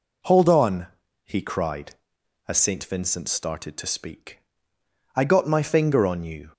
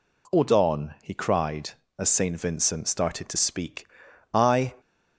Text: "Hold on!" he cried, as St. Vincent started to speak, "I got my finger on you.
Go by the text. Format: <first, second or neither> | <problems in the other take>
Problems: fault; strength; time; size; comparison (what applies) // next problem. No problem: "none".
first | stops before "got my finger on you"; at 4.7 s